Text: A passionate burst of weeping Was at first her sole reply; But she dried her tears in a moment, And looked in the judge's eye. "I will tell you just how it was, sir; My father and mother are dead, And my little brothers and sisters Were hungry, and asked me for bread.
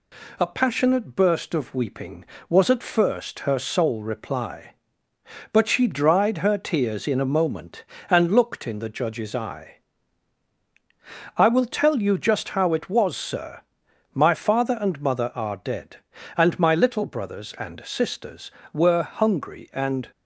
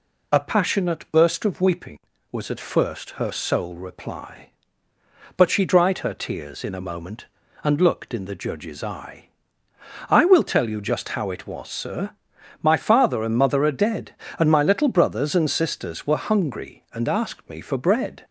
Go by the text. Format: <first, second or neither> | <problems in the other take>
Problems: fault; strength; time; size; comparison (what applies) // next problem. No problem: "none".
second | stops before "asked me for bread"; at 20.1 s